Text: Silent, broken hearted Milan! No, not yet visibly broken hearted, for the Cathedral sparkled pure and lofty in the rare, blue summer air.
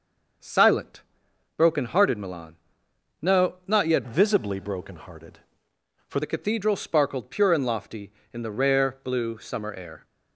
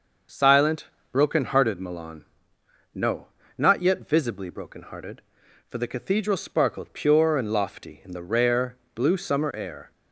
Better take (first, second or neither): second